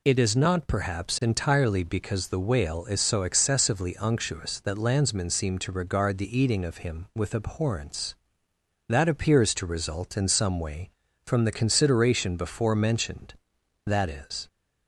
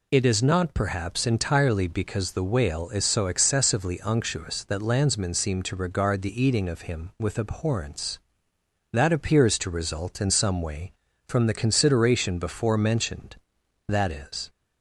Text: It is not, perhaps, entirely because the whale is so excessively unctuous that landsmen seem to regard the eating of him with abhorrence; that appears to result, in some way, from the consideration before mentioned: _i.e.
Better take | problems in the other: neither | none

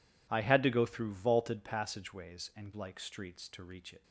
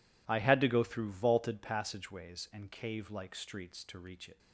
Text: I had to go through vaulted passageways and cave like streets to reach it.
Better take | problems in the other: second | skips "cave"; at 2.7 s

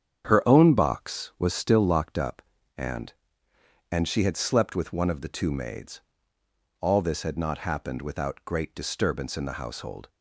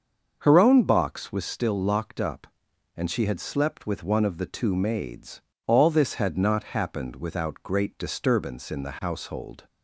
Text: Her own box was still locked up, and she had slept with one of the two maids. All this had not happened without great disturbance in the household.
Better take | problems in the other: second | starts louder than the rest; strong; until 1.2 s; 8.5 dB; also in the second // says "and" twice; at 3.9 s

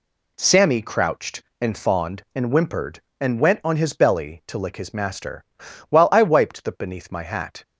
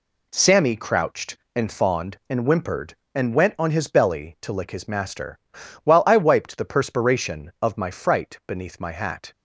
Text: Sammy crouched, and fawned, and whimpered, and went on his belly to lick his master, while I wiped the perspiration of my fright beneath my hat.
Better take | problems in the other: second | skips "perspiration of my fright"; at 6.7 s

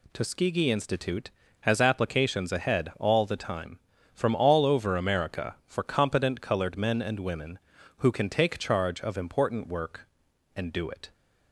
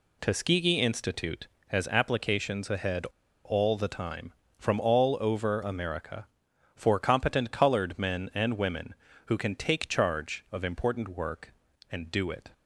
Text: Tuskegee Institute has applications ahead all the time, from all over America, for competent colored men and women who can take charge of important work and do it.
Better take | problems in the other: first | pauses between "ahead" and "all"; at 3.0 s; 0.39 s long

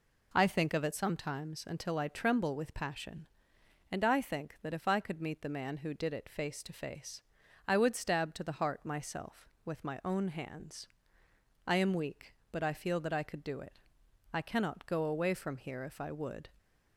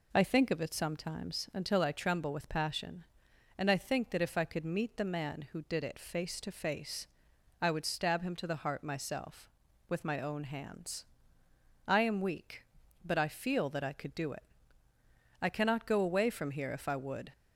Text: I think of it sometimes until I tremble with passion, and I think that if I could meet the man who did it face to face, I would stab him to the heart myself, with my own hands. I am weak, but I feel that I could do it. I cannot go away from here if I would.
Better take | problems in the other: second | skips "him"; at 8.3 s

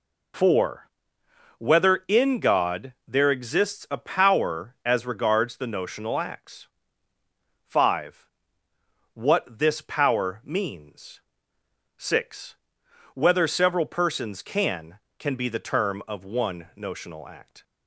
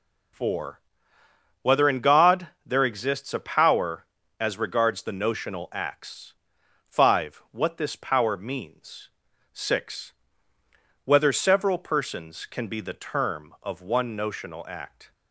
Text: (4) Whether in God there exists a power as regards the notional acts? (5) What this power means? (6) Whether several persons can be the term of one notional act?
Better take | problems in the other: second | pauses between "God" and "there"; slight; at 2.9 s; 0.16 s long; slight in the second // says "can" twice; at 15.1 s

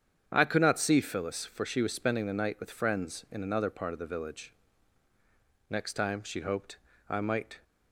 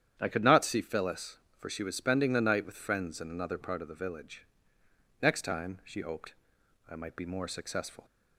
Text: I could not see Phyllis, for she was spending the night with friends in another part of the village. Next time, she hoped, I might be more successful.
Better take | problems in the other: second | starts louder than the rest; strong; until 1.3 s; 8 dB; strong in the second // stops before "be more successful"; at 7.6 s

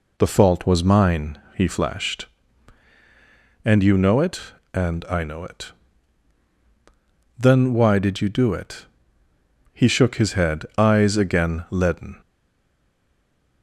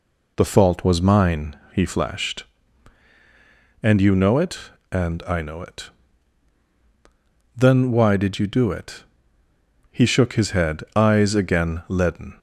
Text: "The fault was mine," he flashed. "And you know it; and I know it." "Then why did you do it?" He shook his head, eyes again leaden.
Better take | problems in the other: second | stays silent after the last word; noticeable; from 12.2 s on; 1.4 s long

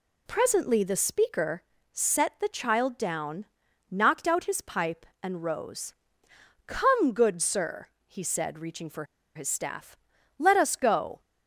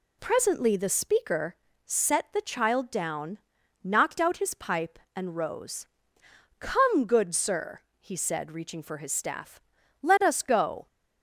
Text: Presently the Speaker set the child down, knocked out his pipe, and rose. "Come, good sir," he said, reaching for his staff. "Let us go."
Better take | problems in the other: second | pauses between "Speaker" and "set"; slight; at 1.6 s; 0.30 s long; slight in the second // pauses between "for" and "his"; slight; at 9.0 s; 0.30 s long

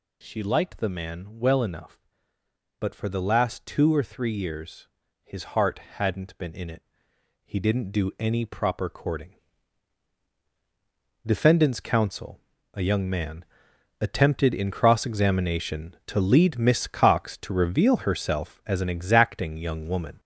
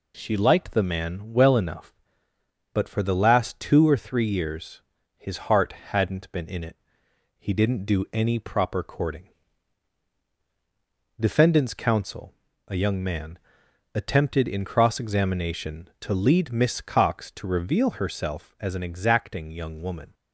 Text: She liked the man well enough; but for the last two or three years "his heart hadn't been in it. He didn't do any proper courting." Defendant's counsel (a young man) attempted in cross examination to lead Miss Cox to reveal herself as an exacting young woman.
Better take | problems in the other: second | gets louder; noticeable; throughout; 5 dB // pauses between "years" and "his"; at 4.8 s; 0.38 s long; also in the second // pauses between "heart" and "hadn't"; slight; at 5.7 s; 0.18 s long; slight in the second

